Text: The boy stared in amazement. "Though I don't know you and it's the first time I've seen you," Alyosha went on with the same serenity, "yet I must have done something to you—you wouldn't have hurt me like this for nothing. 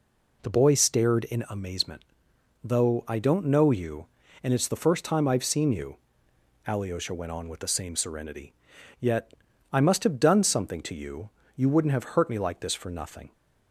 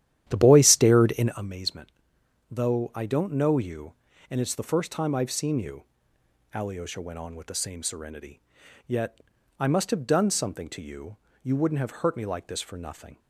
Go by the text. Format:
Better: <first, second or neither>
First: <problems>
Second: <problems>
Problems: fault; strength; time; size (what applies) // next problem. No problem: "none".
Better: first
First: pauses between "yet" and "I"; slight; at 9.3 s; 0.36 s long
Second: starts louder than the rest; strong; until 1.6 s; 11.5 dB // pauses between "yet" and "I"; slight; at 9.2 s; 0.36 s long